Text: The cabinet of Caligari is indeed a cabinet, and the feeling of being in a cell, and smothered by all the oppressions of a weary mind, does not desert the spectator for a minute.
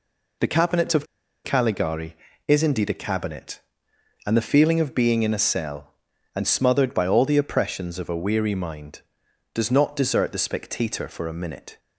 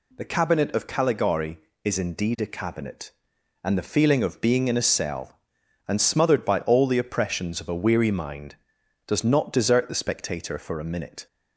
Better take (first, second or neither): second